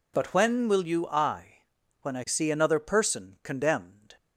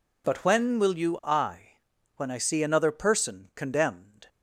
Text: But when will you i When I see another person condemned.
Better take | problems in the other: neither | pauses between "i" and "When"; noticeable; the same in both

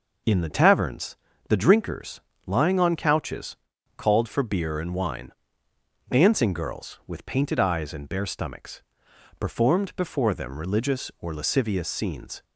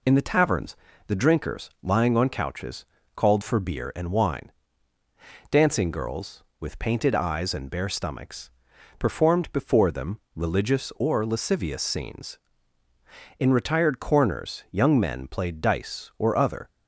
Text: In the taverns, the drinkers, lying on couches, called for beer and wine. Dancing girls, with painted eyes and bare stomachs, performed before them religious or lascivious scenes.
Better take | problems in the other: first | pauses between "them" and "religious"; slight; at 10.1 s; 0.16 s long // goes on to say "In retired corners young men played dice or other"; strong; from 13.3 s on; 3.3 s long

